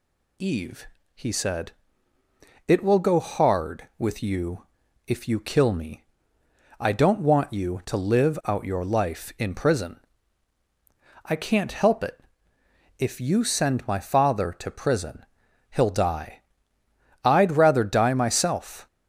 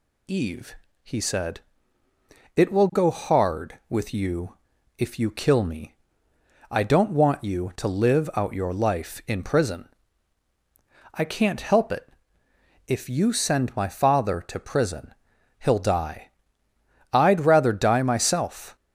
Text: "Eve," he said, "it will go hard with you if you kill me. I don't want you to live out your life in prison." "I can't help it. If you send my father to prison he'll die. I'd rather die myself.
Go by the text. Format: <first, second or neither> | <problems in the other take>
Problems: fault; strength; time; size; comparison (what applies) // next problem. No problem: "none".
neither | pauses between "you" and "if"; the same in both // pauses between "prison" and "he'll"; noticeable; the same in both